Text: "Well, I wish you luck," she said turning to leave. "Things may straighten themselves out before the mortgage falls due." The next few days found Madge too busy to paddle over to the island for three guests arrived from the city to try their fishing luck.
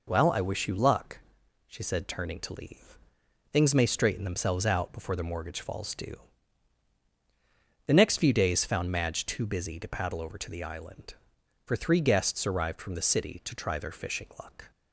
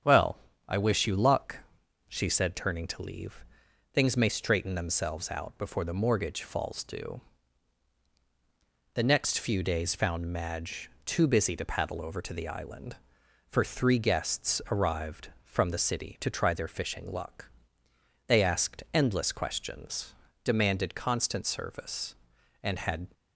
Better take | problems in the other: first | starts louder than the rest; strong; until 1.3 s; 8.5 dB // pauses between "Madge" and "too"; slight; at 10.8 s; 0.16 s long // goes on to say "They asked endless questions demanded constant service and had"; strong; from 18.2 s on; 4.8 s long

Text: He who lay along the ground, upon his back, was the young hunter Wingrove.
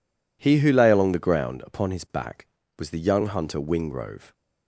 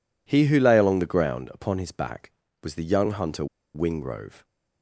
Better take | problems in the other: first | pauses between "hunter" and "Wingrove"; slight; at 3.4 s; 0.29 s long

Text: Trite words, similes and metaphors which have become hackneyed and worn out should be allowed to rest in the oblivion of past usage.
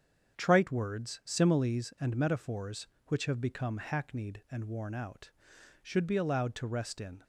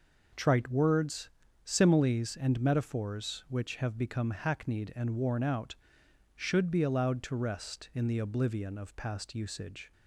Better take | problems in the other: second | starts louder than the rest; strong; until 1.3 s; 7.5 dB // stops before "the oblivion of past usage"; at 7.2 s

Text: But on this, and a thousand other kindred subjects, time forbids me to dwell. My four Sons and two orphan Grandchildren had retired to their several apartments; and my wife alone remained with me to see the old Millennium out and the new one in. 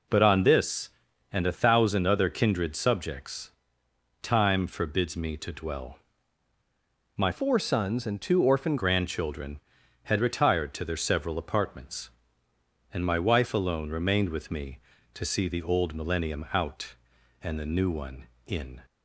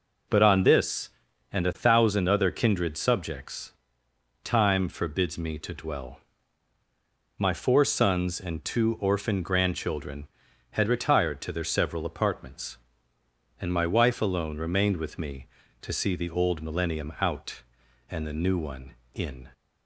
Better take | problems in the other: second | changes voice from "four" to "orphan"; from 7.3 to 8.7 s; 1.4 s long

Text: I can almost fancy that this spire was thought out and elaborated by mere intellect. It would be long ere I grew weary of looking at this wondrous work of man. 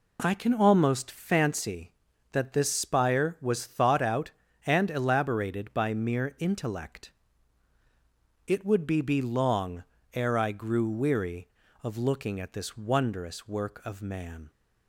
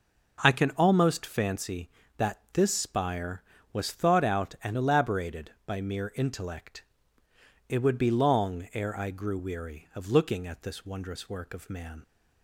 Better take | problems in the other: second | says "be" twice; at 9.0 s // pauses between "long" and "ere"; slight; at 9.8 s; 0.30 s long

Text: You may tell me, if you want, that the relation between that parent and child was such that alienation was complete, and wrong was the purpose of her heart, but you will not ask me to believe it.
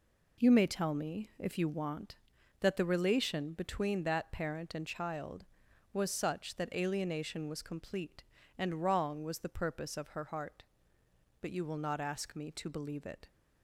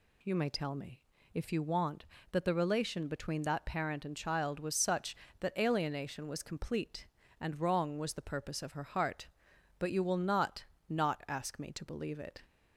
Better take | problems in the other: first | says "not" twice; at 10.8 s

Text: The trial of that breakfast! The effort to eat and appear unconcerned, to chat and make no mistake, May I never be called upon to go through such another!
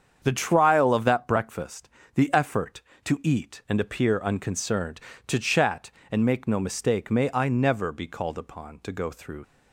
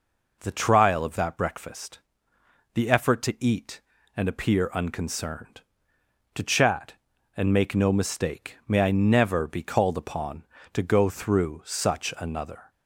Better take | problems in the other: second | starts louder than the rest; strong; until 1.2 s; 7.5 dB // stops before "such another"; at 9.4 s

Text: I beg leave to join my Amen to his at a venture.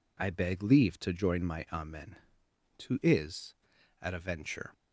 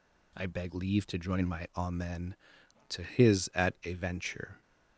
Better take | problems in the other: second | says "is" for "his"; at 3.0 s

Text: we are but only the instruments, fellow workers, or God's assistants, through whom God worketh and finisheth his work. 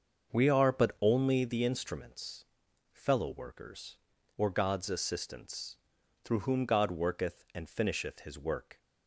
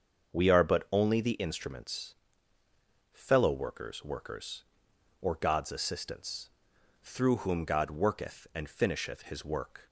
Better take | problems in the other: first | starts louder than the rest; until 1.4 s; 7 dB; also in the first // says "workers" twice; at 4.0 s

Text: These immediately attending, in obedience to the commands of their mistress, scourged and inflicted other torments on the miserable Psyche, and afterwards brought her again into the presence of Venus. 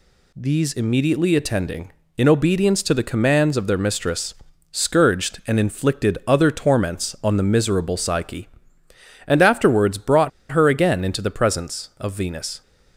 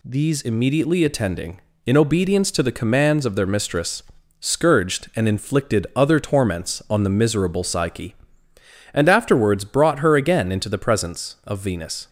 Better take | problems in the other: second | pauses between "brought" and "her"; slight; at 10.2 s; 0.21 s long

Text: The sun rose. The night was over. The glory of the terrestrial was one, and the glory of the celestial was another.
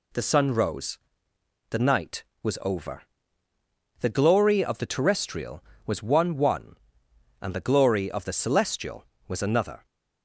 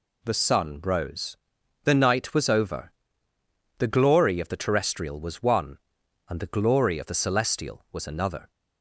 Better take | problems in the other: second | says "one" twice; at 6.3 s

